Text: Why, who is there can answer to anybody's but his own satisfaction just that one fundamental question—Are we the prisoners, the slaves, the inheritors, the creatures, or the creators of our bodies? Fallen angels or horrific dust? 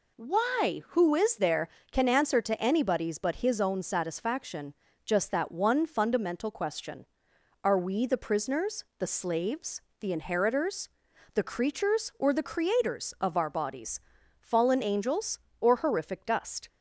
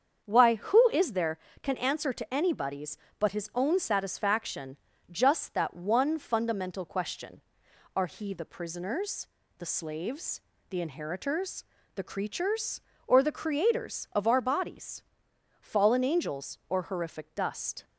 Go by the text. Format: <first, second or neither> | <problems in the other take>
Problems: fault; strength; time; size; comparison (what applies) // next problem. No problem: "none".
first | starts louder than the rest; strong; until 1.2 s; 7.5 dB // pauses between "satisfaction" and "just"; slight; at 4.7 s; 0.34 s long; slight in the first // says "he" for "we"; at 8.0 s